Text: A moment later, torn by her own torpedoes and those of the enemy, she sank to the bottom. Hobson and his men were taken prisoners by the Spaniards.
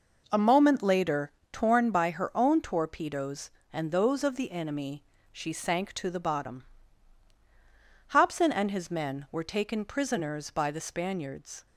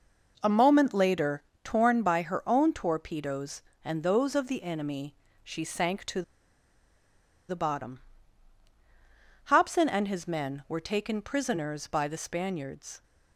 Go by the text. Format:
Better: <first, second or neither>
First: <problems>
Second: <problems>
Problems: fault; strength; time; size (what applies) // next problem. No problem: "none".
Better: first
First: none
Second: pauses between "to" and "the"; strong; at 6.2 s; 1.2 s long